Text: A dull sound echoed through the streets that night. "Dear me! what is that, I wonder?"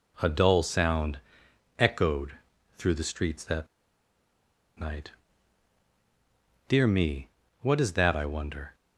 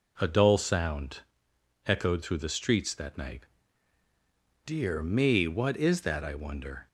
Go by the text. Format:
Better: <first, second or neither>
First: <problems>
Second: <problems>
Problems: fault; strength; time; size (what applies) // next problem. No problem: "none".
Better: second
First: pauses between "sound" and "echoed"; noticeable; at 1.1 s; 0.58 s long // pauses between "echoed" and "through"; at 2.3 s; 0.40 s long // pauses between "that" and "night"; at 3.6 s; 1.1 s long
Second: pauses between "sound" and "echoed"; noticeable; at 1.2 s; 0.66 s long